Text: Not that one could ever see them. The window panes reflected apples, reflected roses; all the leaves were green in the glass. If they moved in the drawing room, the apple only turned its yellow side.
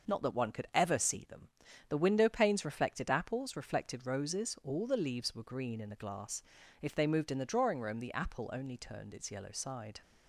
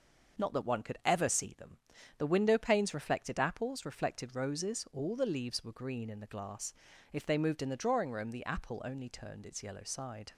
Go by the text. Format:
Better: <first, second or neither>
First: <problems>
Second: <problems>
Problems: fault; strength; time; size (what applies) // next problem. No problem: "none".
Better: neither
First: none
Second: none